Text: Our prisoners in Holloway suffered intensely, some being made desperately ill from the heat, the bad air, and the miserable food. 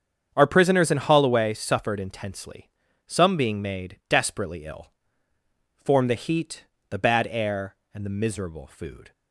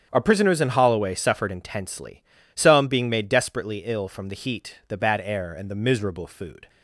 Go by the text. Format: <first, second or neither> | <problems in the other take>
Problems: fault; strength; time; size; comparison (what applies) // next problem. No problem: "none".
second | starts louder than the rest; strong; until 1.3 s; 7.5 dB; strong in the second // says "form" for "from"; at 5.8 s